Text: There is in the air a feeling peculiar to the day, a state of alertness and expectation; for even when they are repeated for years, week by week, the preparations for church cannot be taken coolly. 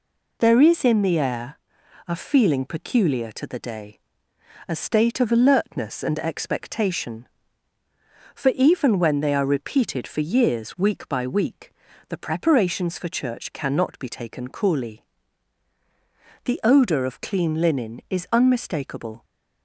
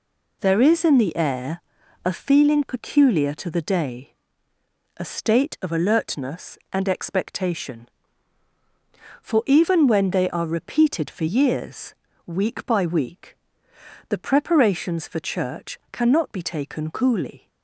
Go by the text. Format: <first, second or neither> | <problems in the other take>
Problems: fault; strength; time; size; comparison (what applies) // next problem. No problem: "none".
second | pauses between "air" and "a"; noticeable; at 1.5 s; 0.48 s long; also in the second // goes on to say "The odour of clean linen is unmistakable"; strong; from 16.4 s on; 2.8 s long